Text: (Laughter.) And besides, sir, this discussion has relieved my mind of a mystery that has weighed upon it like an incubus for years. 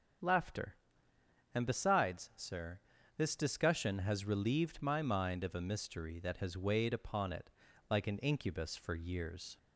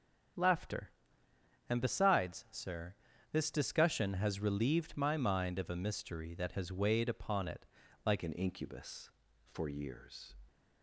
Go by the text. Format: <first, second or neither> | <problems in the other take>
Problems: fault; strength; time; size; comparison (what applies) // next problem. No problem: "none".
first | starts louder than the rest; strong; until 2.1 s; 7.5 dB; strong in the first // pauses between "it" and "like"; at 7.6 s; 0.38 s long; also in the first // changes voice at "an"; from 8.2 s on; 2.1 s long